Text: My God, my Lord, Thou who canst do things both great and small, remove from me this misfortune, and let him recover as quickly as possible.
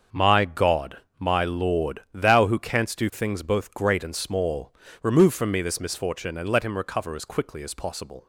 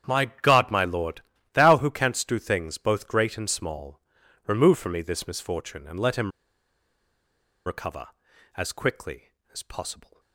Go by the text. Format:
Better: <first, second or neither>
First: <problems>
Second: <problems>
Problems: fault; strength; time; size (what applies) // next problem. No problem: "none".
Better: first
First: starts louder than the rest; until 1.3 s; 6.5 dB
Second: starts louder than the rest; strong; until 1.2 s; 9 dB // pauses between "him" and "recover"; strong; at 6.3 s; 1.3 s long